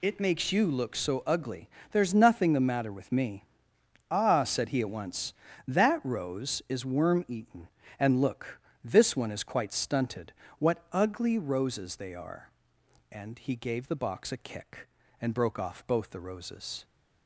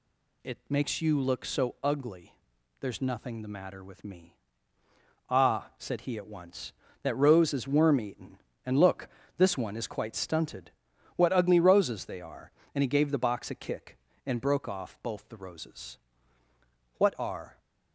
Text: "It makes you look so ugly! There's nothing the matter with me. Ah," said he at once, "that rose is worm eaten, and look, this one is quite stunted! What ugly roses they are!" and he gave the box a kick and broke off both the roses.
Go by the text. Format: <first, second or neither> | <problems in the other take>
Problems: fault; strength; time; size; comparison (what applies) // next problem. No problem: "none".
first | goes on to say "What are"; noticeable; from 16.9 s on; 0.62 s long